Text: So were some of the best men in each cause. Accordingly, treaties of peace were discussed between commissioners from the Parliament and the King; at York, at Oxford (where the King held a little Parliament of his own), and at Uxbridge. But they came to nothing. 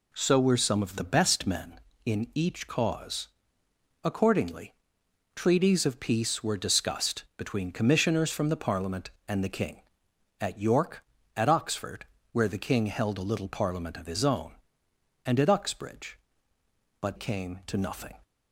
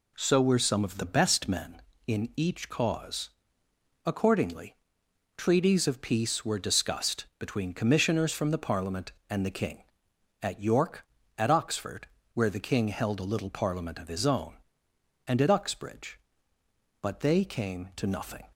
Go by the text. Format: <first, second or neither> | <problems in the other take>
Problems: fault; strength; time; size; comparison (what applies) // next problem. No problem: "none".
second | skips "they"; at 17.1 s